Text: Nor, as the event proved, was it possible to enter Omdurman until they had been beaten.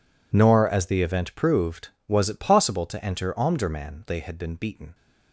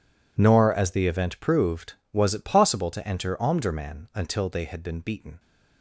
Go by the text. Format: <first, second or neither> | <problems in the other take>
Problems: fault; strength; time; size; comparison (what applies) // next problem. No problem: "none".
second | skips "until"; at 4.0 s